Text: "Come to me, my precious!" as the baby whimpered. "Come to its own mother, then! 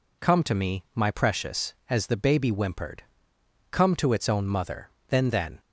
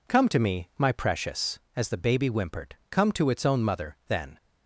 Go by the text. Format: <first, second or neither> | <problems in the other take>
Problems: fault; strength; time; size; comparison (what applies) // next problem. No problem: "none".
second | says "then" twice; at 5.2 s